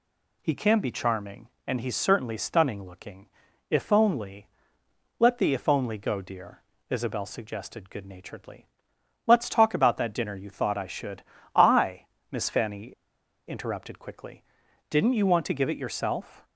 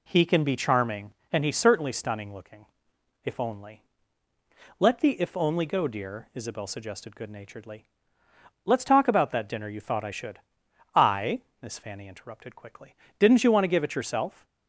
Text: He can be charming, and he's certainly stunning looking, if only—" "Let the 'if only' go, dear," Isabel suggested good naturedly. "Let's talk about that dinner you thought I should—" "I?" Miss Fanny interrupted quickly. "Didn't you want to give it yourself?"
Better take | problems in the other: second | pauses between "Fanny" and "interrupted"; noticeable; at 12.8 s; 0.60 s long

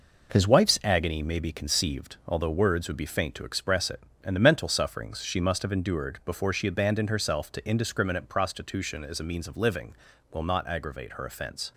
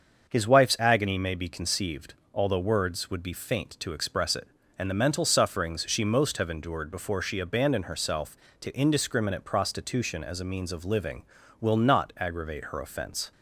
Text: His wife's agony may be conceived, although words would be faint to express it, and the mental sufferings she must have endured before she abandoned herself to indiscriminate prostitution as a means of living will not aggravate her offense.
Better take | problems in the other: first | starts louder than the rest; until 1.3 s; 6.5 dB // says "most" for "must"; at 6.0 s

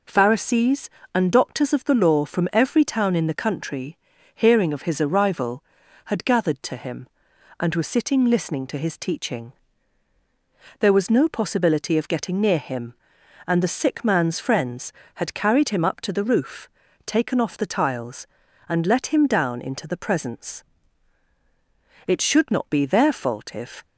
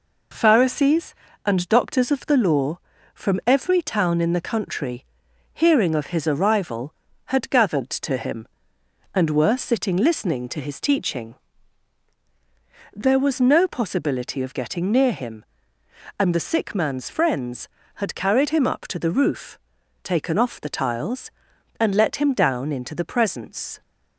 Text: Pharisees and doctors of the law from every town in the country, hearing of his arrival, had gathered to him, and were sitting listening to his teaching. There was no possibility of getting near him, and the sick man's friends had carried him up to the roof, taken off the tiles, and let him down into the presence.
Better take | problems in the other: second | goes on to say "It should not be their fault if"; strong; from 22.0 s on; 1.7 s long

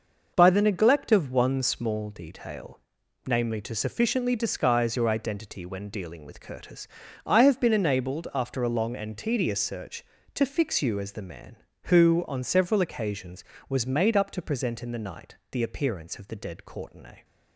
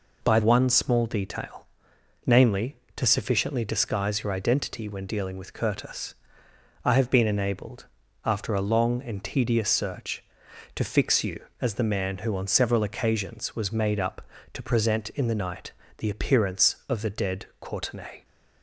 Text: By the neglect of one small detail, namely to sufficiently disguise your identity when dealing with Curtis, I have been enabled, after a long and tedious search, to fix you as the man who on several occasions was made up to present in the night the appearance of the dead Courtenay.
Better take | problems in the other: first | skips "the neglect of"; at 0.4 s // pauses between "night" and "the"; slight; at 15.7 s; 0.28 s long

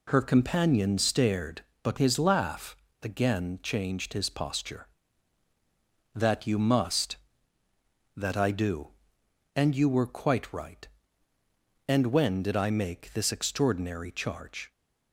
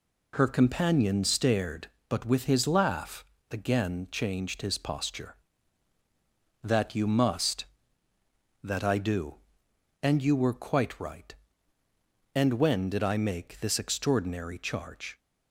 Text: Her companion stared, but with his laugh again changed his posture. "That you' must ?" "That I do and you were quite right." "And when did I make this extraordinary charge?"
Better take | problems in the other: second | skips "with"; at 1.9 s // pauses between "laugh" and "again"; slight; at 2.7 s; 0.28 s long; slight in the second

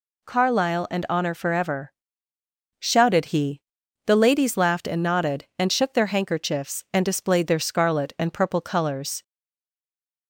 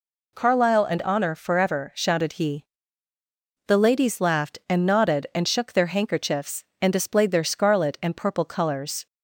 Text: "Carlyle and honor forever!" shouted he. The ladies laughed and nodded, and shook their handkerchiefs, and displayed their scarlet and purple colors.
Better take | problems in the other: second | stays silent after the last word; from 9.2 s on; 1.0 s long

